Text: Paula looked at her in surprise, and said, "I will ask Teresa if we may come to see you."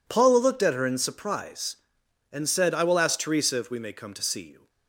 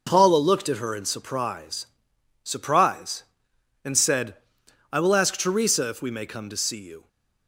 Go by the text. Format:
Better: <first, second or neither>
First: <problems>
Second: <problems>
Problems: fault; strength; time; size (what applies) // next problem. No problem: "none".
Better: first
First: none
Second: says "surprise" twice; at 2.4 s